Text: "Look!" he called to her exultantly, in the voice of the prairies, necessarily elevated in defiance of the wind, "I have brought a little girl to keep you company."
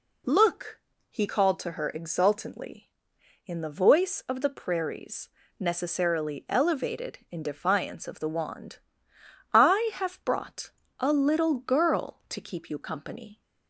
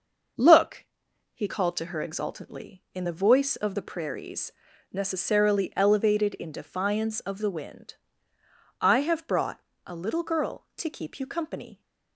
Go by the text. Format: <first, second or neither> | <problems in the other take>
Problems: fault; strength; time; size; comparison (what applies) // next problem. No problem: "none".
second | says "wand" for "wind"; at 8.2 s // pauses between "brought" and "a"; slight; at 10.7 s; 0.26 s long; slight in the second